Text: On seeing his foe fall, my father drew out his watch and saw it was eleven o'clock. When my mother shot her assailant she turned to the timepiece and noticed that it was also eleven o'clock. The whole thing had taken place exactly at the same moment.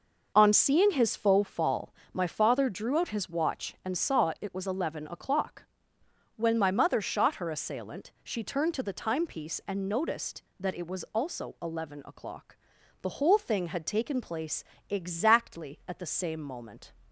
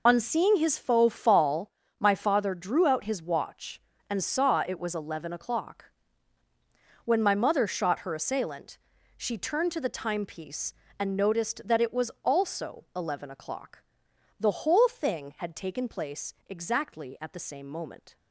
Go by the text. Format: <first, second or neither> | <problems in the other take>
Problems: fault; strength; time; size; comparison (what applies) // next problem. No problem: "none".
first | loses the start of "On"; at 0.0 s; 45 ms // pauses between "assailant" and "she"; at 8.7 s; 0.38 s long // pauses between "place" and "exactly"; slight; at 16.3 s; 0.16 s long; slight in the first